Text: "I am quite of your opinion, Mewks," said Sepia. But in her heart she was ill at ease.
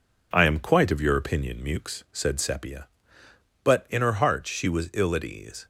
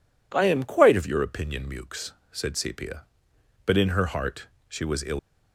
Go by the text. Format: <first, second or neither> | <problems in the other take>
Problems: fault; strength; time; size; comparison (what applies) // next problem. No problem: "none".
first | pauses between "heart" and "she"; slight; at 4.4 s; 0.20 s long // stops before "at ease"; at 5.1 s